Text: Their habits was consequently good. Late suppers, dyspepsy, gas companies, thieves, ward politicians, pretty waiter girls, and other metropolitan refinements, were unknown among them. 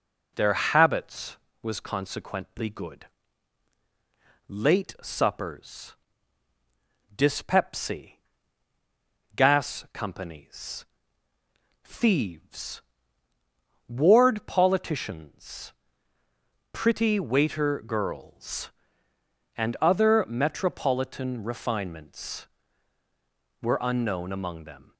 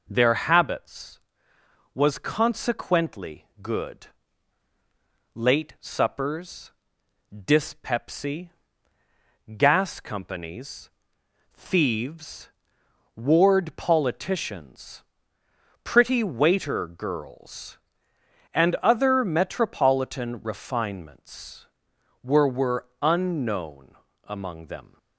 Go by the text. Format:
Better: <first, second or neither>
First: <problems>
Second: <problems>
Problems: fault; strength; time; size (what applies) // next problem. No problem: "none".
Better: first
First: none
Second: says "were" twice; at 22.4 s // pauses between "unknown" and "among"; slight; at 23.9 s; 0.28 s long